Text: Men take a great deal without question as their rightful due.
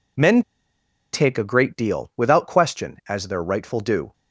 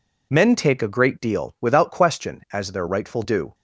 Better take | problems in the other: second | pauses between "Men" and "take"; noticeable; at 0.4 s; 0.71 s long

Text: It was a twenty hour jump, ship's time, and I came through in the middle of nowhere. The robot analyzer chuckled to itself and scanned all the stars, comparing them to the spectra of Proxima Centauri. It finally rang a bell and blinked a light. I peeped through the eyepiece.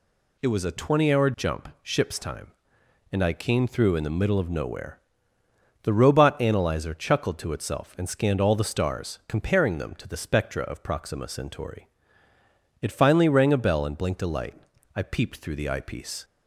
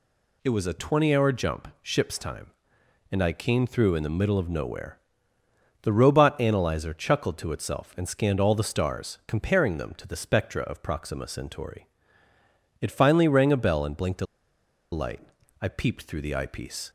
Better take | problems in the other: first | pauses between "a" and "light"; noticeable; at 14.2 s; 0.66 s long

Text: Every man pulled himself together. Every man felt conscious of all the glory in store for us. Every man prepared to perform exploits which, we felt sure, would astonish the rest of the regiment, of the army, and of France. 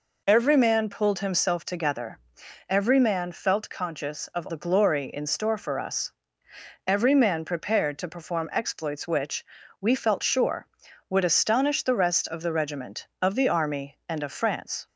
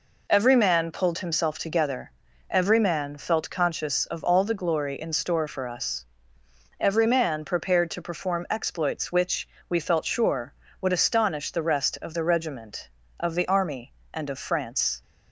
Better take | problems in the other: second | skips "all"; at 4.4 s

